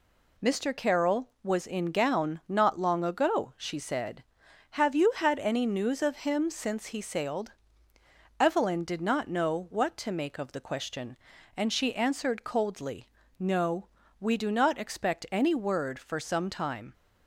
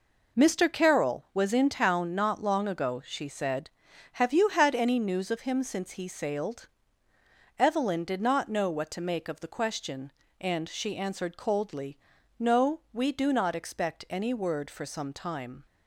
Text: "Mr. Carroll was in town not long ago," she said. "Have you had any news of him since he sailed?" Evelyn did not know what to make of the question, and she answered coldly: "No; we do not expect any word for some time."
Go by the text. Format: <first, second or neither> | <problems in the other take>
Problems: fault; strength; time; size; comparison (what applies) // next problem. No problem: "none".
second | says "gown" for "town"; at 1.9 s